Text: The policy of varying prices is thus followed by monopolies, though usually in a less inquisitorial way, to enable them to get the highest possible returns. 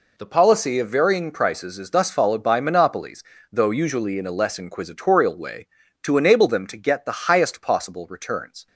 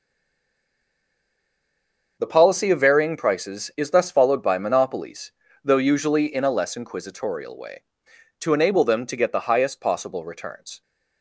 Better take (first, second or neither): first